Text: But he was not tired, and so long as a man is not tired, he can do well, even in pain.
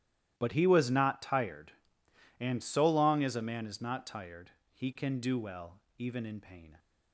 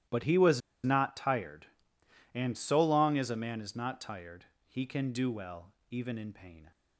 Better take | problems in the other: first | starts louder than the rest; strong; until 1.3 s; 13 dB; strong in the first // pauses between "was" and "not"; slight; at 0.6 s; 0.24 s long

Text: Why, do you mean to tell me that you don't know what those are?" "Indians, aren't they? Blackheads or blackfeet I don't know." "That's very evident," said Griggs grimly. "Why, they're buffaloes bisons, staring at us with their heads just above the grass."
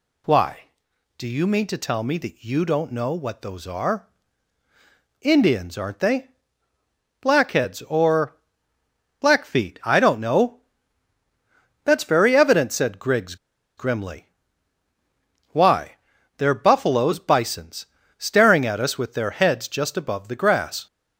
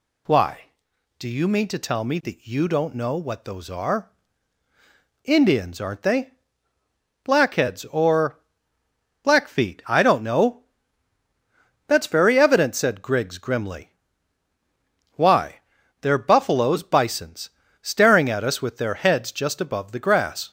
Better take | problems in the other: second | pauses between "or" and "blackfeet"; noticeable; at 8.3 s; 0.84 s long; noticeable in the second // pauses between "Griggs" and "grimly"; at 13.3 s; 0.42 s long

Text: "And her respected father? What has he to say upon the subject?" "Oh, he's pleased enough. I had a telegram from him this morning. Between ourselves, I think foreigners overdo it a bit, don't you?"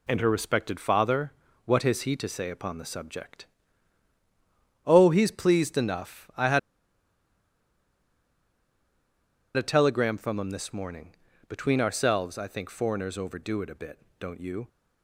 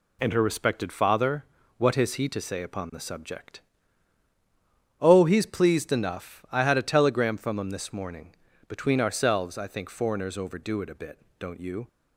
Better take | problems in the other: second | pauses between "had" and "a"; strong; at 6.5 s; 2.9 s long

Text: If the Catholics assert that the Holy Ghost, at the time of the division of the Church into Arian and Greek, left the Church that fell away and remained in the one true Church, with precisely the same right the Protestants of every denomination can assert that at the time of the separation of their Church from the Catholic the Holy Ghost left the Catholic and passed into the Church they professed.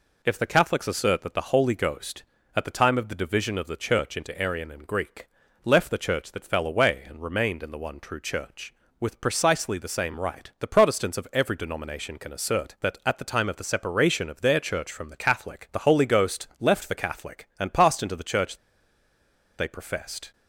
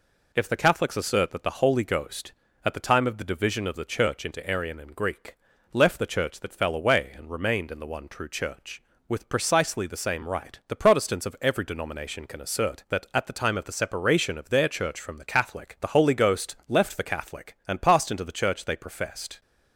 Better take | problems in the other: second | pauses between "Church" and "they"; at 18.5 s; 1.0 s long

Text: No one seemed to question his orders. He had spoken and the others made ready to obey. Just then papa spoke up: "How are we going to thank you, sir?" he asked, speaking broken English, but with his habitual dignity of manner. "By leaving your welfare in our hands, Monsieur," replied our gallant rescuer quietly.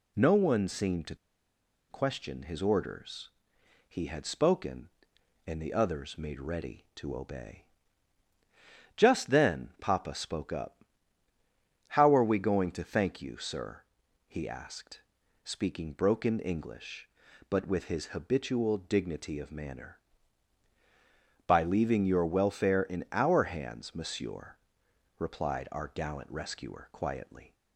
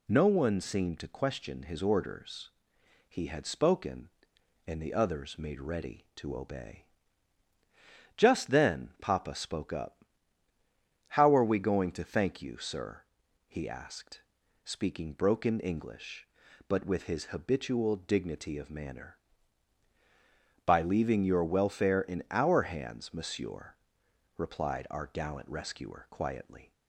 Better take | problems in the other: second | pauses between "to" and "question"; noticeable; at 1.1 s; 0.74 s long

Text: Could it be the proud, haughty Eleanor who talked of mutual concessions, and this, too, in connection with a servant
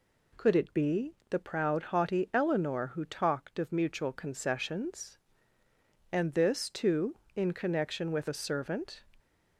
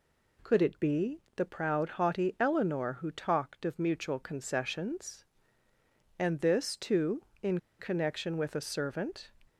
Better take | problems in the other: first | pauses between "be" and "the"; slight; at 1.1 s; 0.16 s long; slight in the first // pauses between "in" and "connection"; slight; at 7.5 s; 0.21 s long

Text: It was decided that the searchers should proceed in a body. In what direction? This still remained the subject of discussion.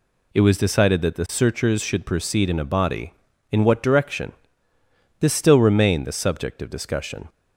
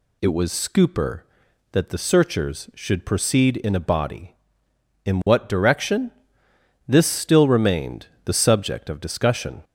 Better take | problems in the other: first | says "scooper" for "decided"; at 0.5 s // pauses between "remained" and "the"; slight; at 8.0 s; 0.16 s long

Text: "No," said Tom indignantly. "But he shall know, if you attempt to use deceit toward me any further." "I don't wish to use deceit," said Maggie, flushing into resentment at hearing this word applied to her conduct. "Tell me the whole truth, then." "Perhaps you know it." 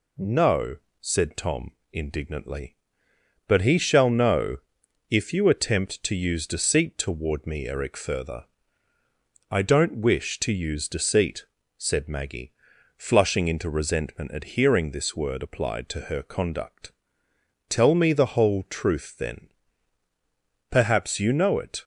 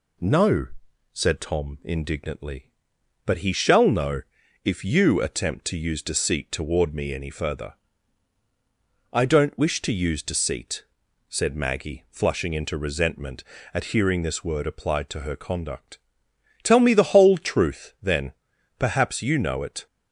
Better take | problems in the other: second | pauses between "Tom" and "indignantly"; slight; at 1.7 s; 0.20 s long // says "eric" for "any"; at 7.6 s

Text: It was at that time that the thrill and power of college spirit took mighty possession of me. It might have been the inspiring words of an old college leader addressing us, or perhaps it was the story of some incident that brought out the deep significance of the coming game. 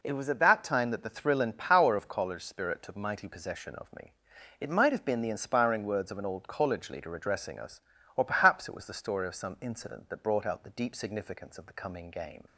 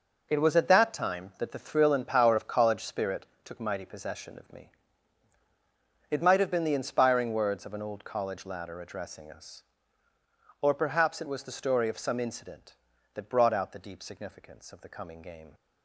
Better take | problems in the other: first | pauses between "spirit" and "took"; slight; at 3.2 s; 0.18 s long // says "ladder" for "leader"; at 8.4 s

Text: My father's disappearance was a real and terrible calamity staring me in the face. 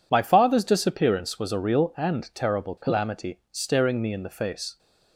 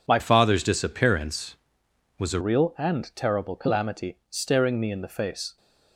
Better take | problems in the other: first | changes voice from "father's" to "a"; from 0.1 to 2.3 s; 2.2 s long

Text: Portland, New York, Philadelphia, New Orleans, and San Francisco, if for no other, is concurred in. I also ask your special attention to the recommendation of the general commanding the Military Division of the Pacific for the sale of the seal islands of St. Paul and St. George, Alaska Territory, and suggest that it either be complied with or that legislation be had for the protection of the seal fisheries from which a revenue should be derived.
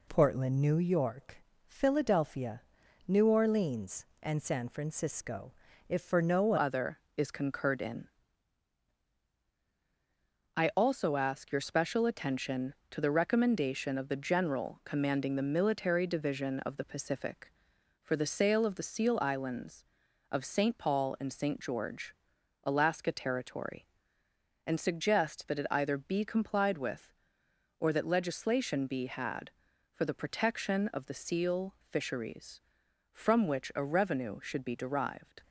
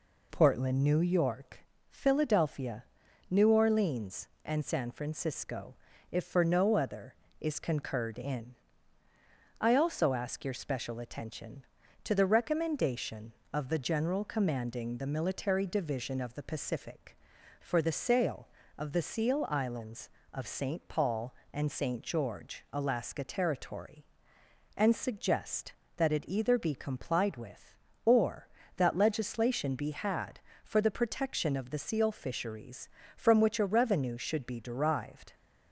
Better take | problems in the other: second | changes voice at "other"; from 6.5 s on; 28.9 s long

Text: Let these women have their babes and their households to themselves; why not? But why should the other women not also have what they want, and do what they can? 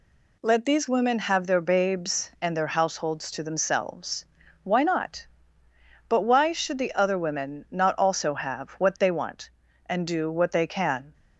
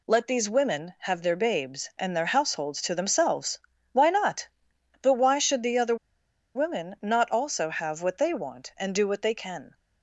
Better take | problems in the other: first | pauses between "other" and "women"; noticeable; at 5.9 s; 0.60 s long

